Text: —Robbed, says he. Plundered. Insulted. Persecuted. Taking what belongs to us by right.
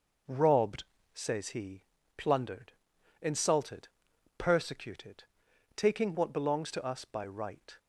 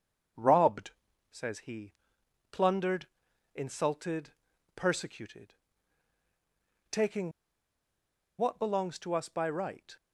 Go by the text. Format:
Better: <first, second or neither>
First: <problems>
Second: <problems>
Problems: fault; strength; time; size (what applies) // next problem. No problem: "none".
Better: first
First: none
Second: starts louder than the rest; until 1.7 s; 7 dB // pauses between "Taking" and "what"; at 7.3 s; 1.0 s long